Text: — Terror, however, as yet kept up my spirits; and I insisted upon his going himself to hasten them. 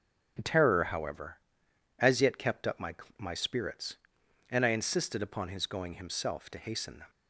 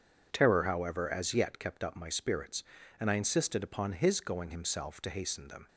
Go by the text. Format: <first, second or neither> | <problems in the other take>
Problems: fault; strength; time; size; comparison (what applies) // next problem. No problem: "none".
second | starts louder than the rest; strong; until 2.0 s; 9.5 dB // says "my" twice; at 3.1 s